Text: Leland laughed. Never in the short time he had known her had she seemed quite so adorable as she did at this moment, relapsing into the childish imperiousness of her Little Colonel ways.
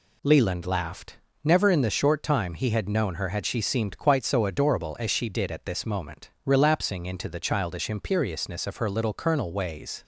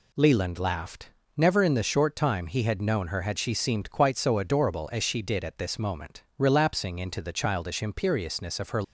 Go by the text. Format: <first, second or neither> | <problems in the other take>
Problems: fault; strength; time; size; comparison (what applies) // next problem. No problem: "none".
first | stops before "Little Colonel ways"; at 8.8 s